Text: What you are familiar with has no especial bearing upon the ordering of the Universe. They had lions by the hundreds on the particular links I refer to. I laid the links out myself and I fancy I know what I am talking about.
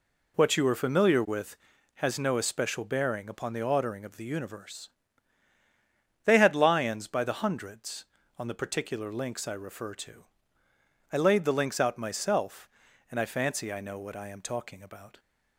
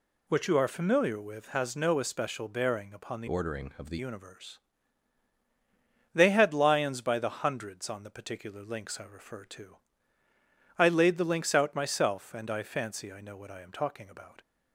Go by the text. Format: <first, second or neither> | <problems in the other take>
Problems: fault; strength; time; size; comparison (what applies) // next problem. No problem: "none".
first | changes voice from "ordering" to "the"; from 3.2 to 3.9 s; 0.7 s long